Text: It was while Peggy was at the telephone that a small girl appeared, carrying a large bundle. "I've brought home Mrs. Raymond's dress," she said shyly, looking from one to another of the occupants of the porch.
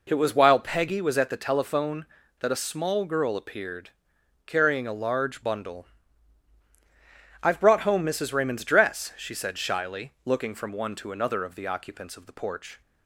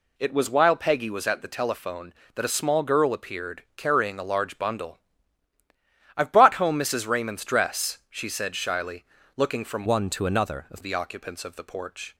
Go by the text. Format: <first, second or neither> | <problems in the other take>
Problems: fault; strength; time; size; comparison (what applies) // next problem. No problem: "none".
first | changes voice from "one" to "of"; from 9.8 to 10.8 s; 1.0 s long